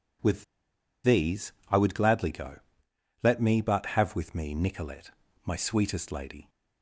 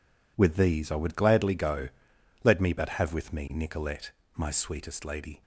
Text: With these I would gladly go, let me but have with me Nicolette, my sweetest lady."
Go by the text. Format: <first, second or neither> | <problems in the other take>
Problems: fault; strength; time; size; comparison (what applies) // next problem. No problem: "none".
second | pauses between "With" and "these"; noticeable; at 0.4 s; 0.60 s long // pauses between "these" and "I"; slight; at 1.5 s; 0.18 s long